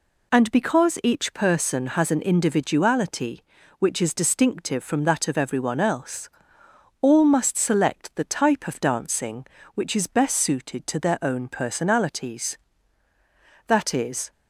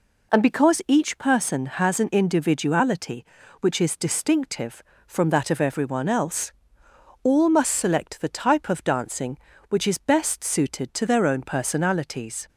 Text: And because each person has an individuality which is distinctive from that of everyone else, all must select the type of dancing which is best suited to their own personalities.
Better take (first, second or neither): second